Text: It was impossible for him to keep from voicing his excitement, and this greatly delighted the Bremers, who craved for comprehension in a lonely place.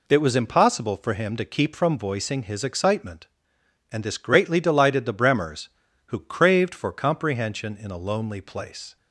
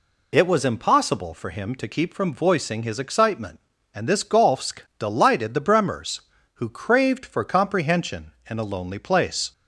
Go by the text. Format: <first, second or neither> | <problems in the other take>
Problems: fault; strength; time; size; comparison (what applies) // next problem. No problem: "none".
first | says "golfsk" for "greatly"; at 4.2 s